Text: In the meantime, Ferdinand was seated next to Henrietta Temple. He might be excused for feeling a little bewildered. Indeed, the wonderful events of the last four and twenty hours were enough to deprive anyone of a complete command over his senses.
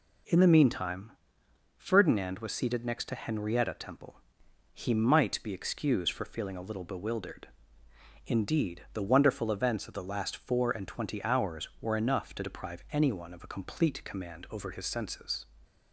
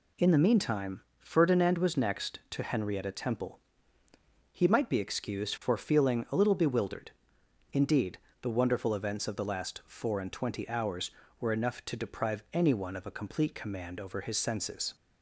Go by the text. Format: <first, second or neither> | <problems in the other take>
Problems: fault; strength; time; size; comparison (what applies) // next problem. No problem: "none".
first | skips "seated"; at 1.9 s